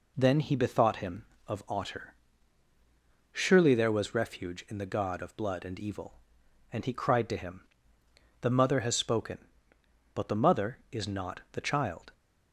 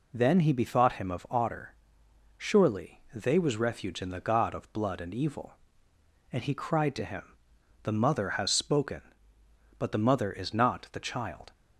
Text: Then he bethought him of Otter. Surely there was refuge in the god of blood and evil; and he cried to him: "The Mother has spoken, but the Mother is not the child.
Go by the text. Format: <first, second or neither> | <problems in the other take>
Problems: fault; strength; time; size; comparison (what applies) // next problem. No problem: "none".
first | says "they" for "there"; at 3.1 s